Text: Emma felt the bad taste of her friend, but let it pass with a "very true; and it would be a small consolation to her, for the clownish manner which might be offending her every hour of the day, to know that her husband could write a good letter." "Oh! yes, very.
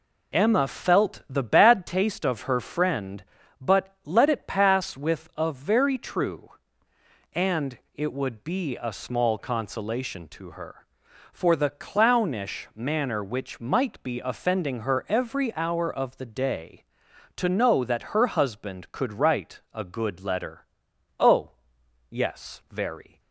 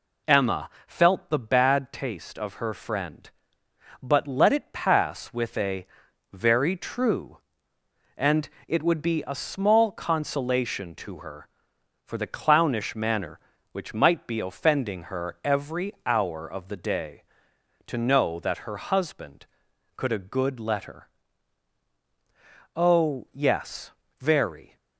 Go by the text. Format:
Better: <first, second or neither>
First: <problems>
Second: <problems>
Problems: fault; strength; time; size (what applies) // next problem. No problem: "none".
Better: first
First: pauses between "and" and "it"; slight; at 7.7 s; 0.16 s long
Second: pauses between "Emma" and "felt"; slight; at 0.6 s; 0.18 s long // pauses between "a" and "very"; noticeable; at 5.8 s; 0.48 s long // pauses between "and" and "it"; slight; at 8.4 s; 0.20 s long // skips "write"; at 20.1 s